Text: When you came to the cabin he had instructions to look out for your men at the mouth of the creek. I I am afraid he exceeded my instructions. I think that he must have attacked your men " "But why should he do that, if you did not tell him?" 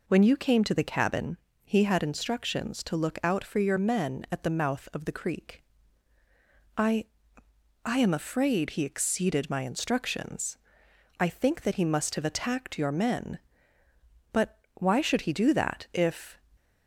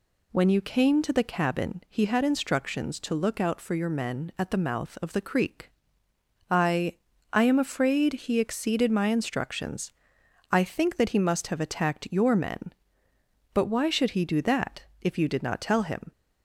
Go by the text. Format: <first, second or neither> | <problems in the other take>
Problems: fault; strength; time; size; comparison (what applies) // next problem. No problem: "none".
second | pauses between "cabin" and "he"; slight; at 1.3 s; 0.28 s long // pauses between "I" and "I"; noticeable; at 7.0 s; 0.80 s long; slight in the second // stops before "you did not tell him"; at 16.5 s